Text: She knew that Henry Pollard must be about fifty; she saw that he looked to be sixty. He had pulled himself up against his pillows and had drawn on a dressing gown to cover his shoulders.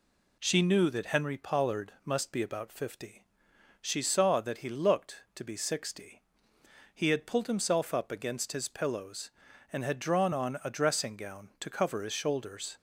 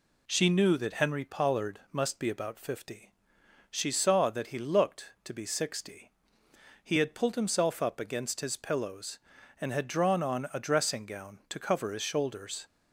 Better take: neither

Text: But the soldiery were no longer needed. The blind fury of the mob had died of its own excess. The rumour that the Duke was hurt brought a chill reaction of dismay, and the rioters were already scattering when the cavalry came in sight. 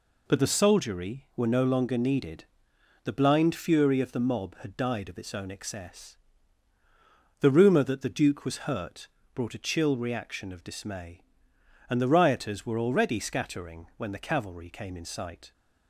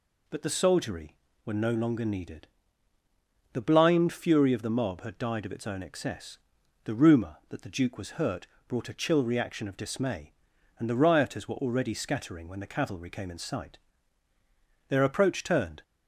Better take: first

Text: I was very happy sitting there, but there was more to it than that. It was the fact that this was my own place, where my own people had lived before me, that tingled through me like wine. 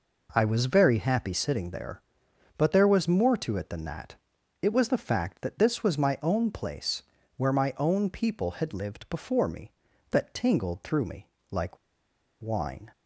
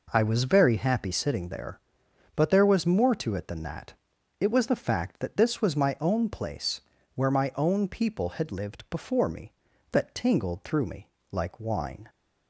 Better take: second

